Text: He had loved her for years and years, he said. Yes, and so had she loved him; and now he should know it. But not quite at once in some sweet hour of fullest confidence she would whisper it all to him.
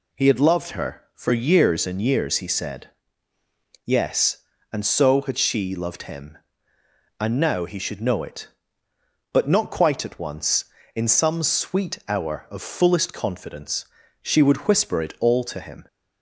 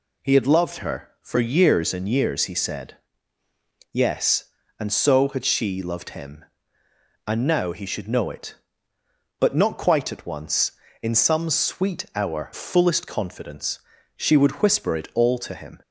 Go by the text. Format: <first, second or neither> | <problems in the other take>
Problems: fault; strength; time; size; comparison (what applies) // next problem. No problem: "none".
first | skips "of"; at 12.5 s // pauses between "confidence" and "she"; slight; at 13.7 s; 0.36 s long; slight in the first